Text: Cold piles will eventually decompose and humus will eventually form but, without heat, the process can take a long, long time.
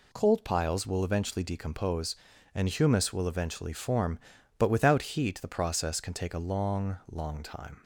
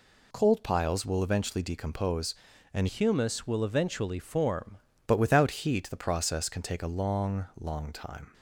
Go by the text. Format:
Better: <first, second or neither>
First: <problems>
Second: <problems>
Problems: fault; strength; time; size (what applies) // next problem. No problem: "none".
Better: first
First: none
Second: changes voice from "humus" to "form"; from 2.8 to 4.7 s; 1.9 s long